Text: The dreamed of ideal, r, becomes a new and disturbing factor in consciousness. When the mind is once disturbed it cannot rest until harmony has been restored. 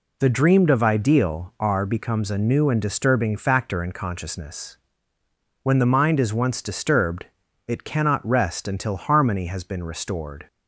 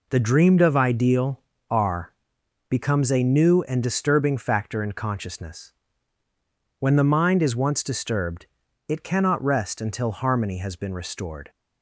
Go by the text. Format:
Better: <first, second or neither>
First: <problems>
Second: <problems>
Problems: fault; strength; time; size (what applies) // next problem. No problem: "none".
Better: neither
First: pauses between "disturbed" and "it"; at 7.2 s; 0.42 s long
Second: pauses between "disturbed" and "it"; at 8.4 s; 0.42 s long